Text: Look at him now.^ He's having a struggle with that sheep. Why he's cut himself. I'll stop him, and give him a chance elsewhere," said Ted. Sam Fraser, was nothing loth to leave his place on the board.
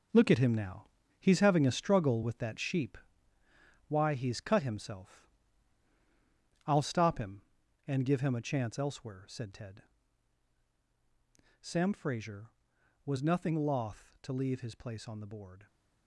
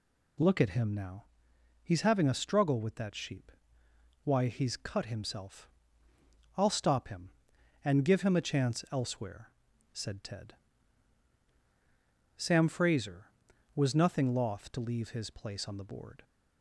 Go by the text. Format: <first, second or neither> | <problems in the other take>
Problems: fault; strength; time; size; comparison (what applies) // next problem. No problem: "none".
second | gets quieter; strong; throughout; 10 dB